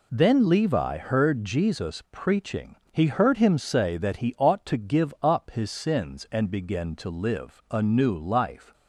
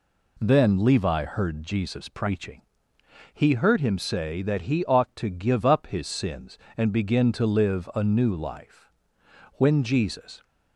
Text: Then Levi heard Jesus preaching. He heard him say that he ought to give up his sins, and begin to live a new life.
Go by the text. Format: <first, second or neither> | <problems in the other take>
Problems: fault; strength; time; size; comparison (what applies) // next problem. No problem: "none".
first | goes on to say "When Jesus"; noticeable; from 9.5 s on; 0.88 s long